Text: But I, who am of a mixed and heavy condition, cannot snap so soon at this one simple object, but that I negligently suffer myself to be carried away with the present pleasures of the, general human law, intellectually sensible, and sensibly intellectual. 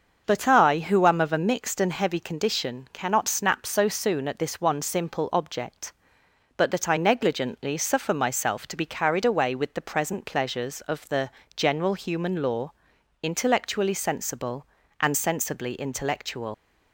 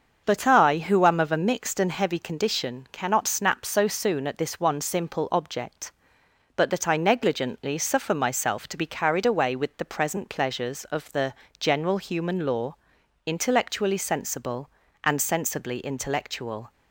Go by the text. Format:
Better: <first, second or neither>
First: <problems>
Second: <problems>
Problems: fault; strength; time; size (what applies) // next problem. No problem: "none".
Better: second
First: starts louder than the rest; until 1.2 s; 6.5 dB // leaves "intellectual" unfinished; at 16.5 s; 130 ms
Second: starts louder than the rest; until 1.2 s; 6.5 dB